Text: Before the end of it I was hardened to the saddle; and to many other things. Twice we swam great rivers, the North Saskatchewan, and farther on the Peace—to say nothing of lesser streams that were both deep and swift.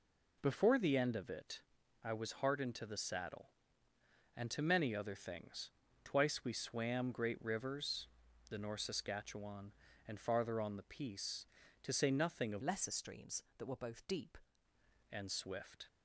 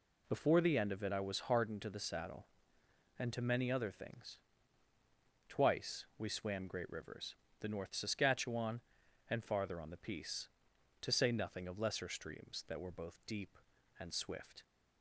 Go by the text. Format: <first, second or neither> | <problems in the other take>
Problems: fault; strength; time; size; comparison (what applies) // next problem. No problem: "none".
second | pauses between "it" and "I"; at 1.6 s; 0.42 s long // changes voice from "lesser" to "deep"; from 12.6 to 14.3 s; 1.7 s long